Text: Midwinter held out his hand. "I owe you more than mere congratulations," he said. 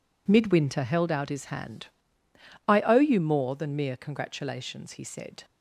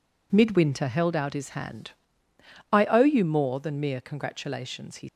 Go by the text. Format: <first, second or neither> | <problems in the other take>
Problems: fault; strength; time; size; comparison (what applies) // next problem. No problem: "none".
first | stops before "said"; at 5.0 s